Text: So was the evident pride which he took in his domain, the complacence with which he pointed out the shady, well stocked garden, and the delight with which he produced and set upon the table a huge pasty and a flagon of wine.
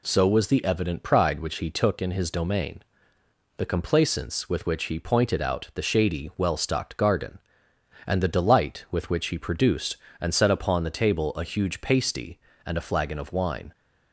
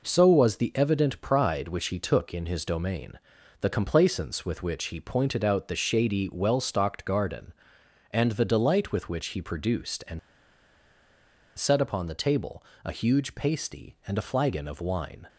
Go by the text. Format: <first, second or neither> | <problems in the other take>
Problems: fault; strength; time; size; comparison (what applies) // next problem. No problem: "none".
first | pauses between "and" and "set"; strong; at 10.1 s; 1.3 s long // pauses between "table" and "a"; slight; at 12.6 s; 0.22 s long